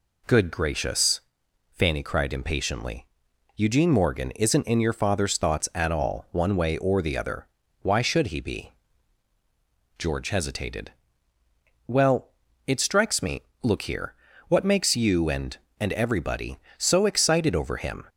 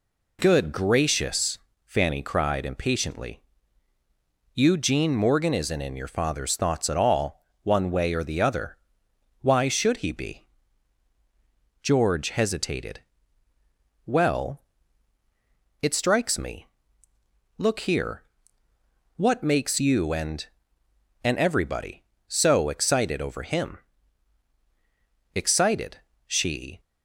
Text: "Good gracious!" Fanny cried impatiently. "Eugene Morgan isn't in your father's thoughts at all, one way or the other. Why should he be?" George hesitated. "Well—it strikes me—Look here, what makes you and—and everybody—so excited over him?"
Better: first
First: none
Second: goes on to say "Excited she"; from 25.3 s on; 1.4 s long

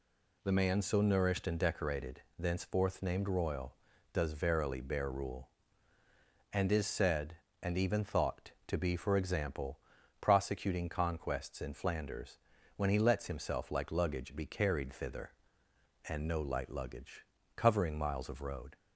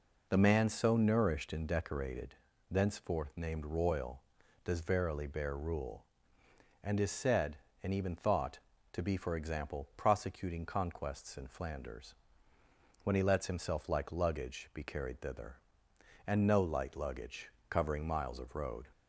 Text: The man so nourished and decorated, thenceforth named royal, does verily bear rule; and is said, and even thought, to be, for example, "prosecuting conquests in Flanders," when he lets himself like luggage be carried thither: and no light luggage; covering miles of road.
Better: neither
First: none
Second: none

